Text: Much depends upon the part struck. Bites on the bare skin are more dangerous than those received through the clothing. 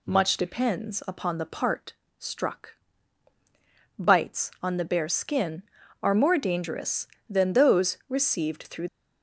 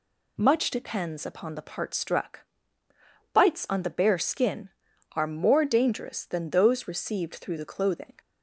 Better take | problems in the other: second | pauses between "part" and "struck"; slight; at 1.9 s; 0.24 s long // stops before "the clothing"; at 8.8 s

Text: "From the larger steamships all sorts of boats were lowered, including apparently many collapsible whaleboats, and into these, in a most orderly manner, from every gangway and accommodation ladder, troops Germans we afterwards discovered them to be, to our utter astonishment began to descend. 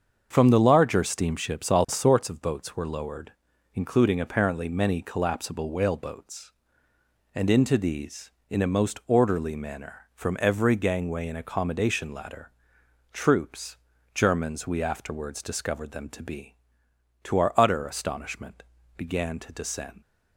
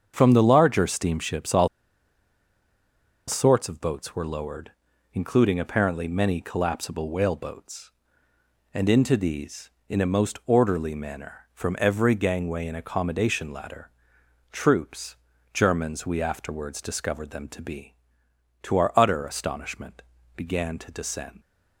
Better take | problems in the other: first | starts louder than the rest; until 1.1 s; 7 dB; also in the first // pauses between "all" and "sorts"; strong; at 1.6 s; 1.6 s long // pauses between "troops" and "Germans"; slight; at 15.1 s; 0.36 s long; slight in the first // pauses between "astonishment" and "began"; slight; at 20.0 s; 0.32 s long; slight in the first

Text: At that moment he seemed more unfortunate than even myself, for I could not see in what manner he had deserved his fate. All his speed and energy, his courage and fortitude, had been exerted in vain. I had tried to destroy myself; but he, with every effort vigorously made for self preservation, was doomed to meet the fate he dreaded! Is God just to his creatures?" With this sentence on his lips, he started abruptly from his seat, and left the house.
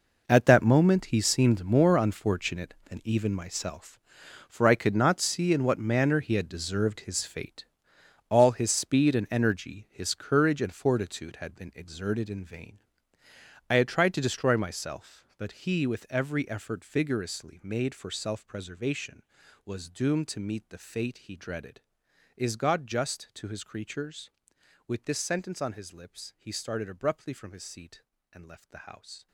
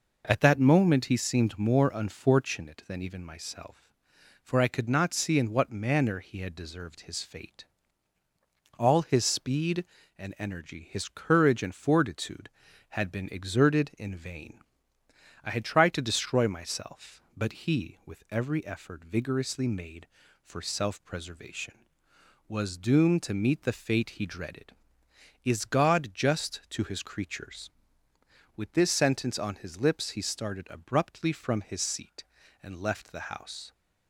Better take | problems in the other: second | gets quieter; strong; throughout; 14.5 dB

